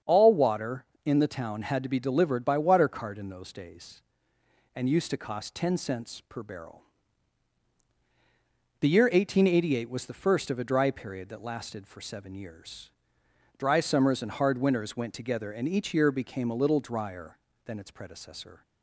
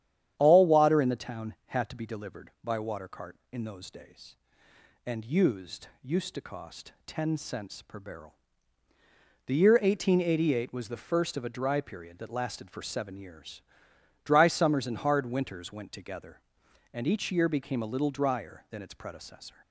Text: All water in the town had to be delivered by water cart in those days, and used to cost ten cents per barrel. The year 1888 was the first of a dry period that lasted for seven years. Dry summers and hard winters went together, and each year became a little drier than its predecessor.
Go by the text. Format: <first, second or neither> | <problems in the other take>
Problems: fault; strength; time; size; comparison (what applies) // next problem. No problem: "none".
first | starts louder than the rest; strong; until 1.3 s; 10 dB; strong in the first // says "used" twice; at 6.0 s